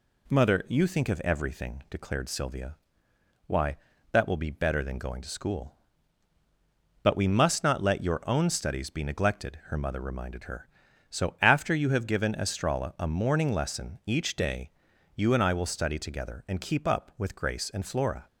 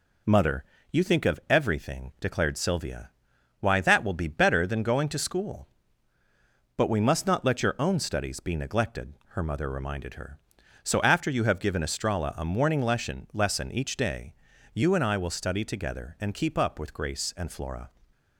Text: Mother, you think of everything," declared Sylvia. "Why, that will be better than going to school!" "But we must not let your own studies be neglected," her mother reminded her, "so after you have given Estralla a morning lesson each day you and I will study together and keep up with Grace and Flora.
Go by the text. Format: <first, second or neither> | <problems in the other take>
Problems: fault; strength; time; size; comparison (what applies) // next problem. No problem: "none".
first | says "lesson" twice; at 13.3 s // pauses between "day" and "you"; at 14.3 s; 0.38 s long; also in the first